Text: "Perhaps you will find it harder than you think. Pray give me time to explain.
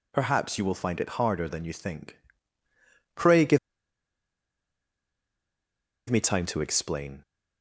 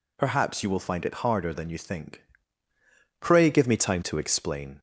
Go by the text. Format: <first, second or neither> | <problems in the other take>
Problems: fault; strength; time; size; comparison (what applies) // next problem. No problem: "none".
second | pauses between "give" and "me"; strong; at 3.5 s; 2.5 s long